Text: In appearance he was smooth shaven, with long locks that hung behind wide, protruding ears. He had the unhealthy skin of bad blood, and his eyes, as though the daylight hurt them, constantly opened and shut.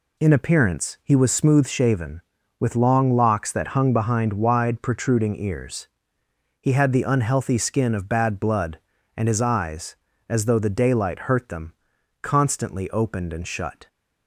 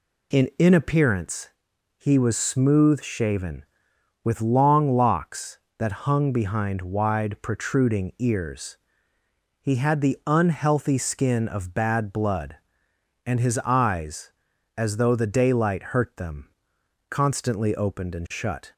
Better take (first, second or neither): first